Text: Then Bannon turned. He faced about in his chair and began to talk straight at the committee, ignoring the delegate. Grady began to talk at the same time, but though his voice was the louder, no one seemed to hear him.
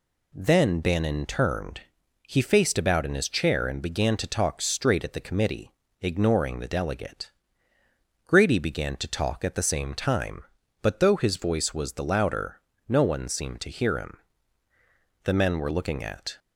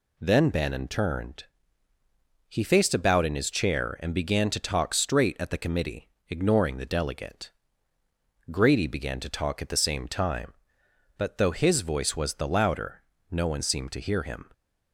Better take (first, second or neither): second